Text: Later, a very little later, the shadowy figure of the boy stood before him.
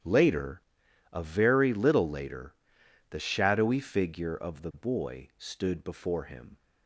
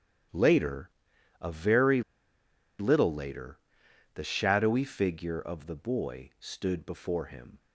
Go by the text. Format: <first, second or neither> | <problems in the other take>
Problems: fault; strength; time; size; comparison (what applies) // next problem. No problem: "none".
first | starts louder than the rest; strong; until 1.8 s; 10.5 dB; strong in the first // pauses between "very" and "little"; noticeable; at 2.0 s; 0.76 s long